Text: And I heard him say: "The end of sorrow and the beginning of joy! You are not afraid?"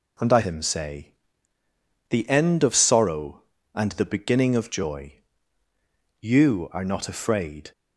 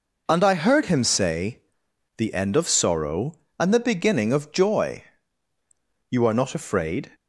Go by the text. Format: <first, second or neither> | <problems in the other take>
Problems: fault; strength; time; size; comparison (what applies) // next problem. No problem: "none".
second | skips "heard"; at 0.4 s